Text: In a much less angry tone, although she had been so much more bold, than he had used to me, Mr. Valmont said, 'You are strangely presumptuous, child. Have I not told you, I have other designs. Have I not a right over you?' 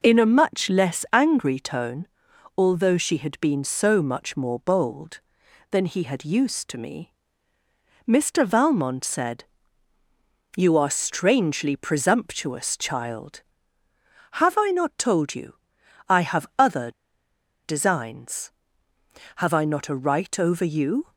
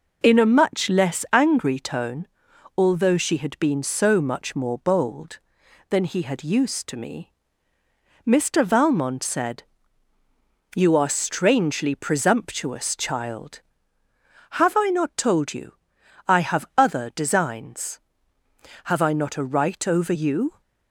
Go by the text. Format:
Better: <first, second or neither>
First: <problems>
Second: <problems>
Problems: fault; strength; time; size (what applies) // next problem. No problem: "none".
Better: second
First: pauses between "other" and "designs"; noticeable; at 16.9 s; 0.73 s long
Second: none